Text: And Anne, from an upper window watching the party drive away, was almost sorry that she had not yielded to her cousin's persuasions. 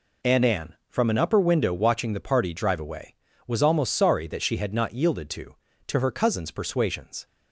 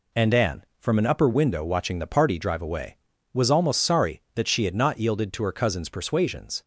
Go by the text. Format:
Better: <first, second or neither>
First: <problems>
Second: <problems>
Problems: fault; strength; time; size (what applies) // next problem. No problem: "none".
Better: second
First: says "to" twice; at 5.8 s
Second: none